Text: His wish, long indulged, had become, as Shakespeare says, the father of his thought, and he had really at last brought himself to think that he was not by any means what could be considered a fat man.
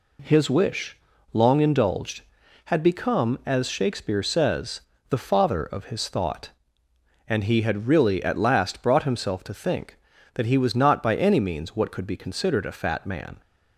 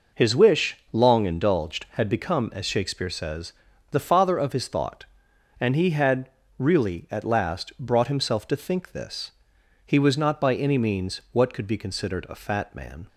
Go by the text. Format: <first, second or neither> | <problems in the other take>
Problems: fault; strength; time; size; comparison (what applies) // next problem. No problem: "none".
first | pauses between "had" and "really"; slight; at 6.2 s; 0.30 s long // says "this" for "that"; at 8.9 s